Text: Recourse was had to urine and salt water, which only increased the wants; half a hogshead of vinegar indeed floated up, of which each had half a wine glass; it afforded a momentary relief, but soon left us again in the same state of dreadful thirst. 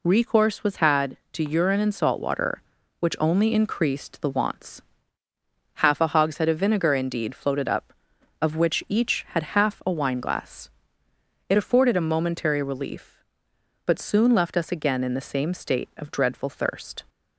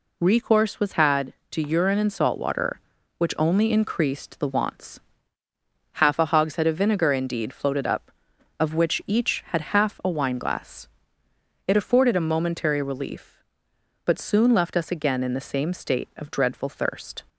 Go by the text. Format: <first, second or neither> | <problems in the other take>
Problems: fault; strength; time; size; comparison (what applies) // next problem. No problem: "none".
neither | none